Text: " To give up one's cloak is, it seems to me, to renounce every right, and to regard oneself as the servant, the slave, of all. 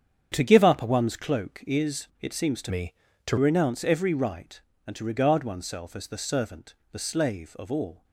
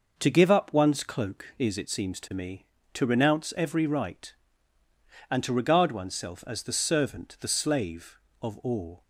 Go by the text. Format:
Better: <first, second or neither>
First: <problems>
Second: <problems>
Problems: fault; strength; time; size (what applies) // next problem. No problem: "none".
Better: second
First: starts louder than the rest; strong; until 1.3 s; 8 dB // changes voice from "me" to "to"; from 2.6 to 3.3 s; 0.7 s long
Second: none